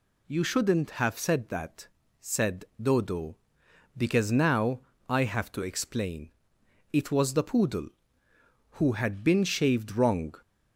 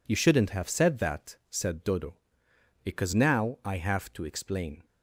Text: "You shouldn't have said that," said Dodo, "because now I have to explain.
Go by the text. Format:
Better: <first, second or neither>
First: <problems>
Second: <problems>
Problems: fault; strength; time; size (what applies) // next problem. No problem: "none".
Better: second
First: pauses between "said" and "Dodo"; slight; at 2.6 s; 0.16 s long // pauses between "now" and "I"; slight; at 4.8 s; 0.28 s long // goes on to say "It was the poodle who had been shaved wrong"; strong; from 6.9 s on; 3.4 s long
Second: none